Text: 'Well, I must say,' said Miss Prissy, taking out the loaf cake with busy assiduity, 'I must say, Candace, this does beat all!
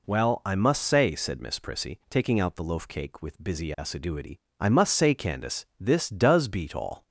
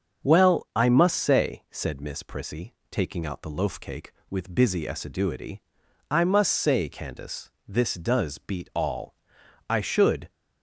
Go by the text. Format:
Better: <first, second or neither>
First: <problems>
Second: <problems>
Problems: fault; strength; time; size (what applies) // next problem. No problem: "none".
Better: first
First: none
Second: starts louder than the rest; until 1.3 s; 7 dB // goes on to say "I should"; noticeable; from 9.6 s on; 0.62 s long